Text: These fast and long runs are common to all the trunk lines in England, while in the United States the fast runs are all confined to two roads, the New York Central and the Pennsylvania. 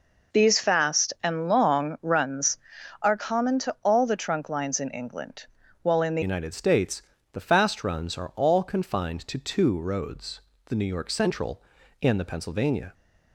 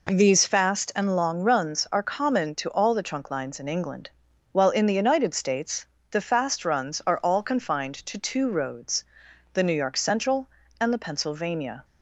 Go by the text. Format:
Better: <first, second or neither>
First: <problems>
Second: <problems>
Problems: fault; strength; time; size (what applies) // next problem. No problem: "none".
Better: second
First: changes voice at "United"; from 6.2 s on; 6.7 s long // pauses between "States" and "the"; slight; at 7.0 s; 0.30 s long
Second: pauses between "States" and "the"; slight; at 5.8 s; 0.26 s long